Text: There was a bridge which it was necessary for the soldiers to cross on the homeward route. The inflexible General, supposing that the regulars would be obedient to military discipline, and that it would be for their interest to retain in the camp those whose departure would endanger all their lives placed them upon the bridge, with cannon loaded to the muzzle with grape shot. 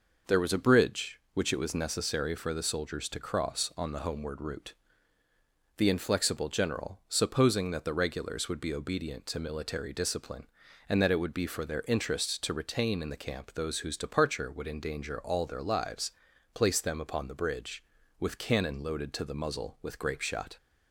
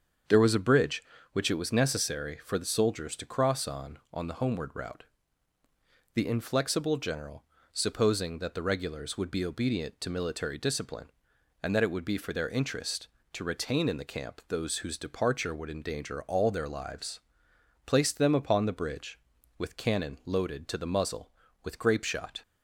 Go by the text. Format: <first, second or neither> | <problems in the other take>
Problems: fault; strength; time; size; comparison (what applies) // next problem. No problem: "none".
first | starts louder than the rest; strong; until 1.6 s; 7 dB // says "on" twice; at 4.1 s // pauses between "lives" and "placed"; noticeable; at 17.1 s; 0.64 s long; also in the first